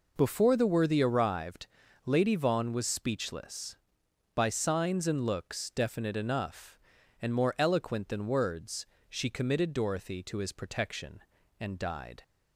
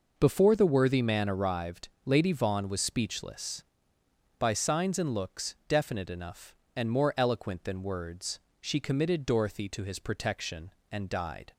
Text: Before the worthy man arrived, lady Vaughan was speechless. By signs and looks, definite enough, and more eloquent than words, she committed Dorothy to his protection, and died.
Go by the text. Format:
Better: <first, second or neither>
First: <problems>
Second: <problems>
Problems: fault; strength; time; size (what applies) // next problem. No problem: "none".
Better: second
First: skips "man"; at 1.0 s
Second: none